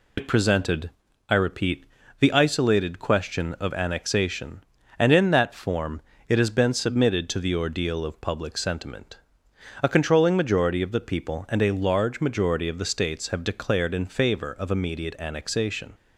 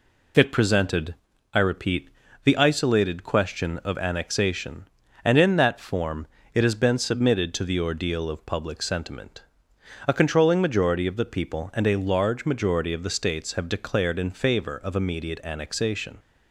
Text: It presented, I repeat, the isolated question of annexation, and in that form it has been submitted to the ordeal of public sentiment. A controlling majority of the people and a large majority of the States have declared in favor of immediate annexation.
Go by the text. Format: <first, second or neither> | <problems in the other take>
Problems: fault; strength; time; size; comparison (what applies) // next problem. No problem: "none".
second | loses the start of "It"; at 0.1 s; 70 ms // pauses between "form" and "it"; slight; at 6.0 s; 0.28 s long; slight in the second